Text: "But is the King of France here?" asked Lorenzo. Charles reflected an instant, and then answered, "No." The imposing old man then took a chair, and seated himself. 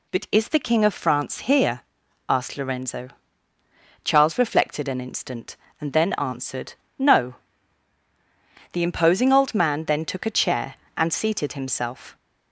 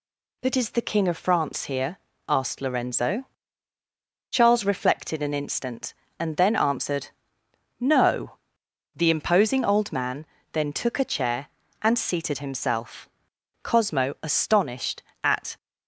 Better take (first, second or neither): first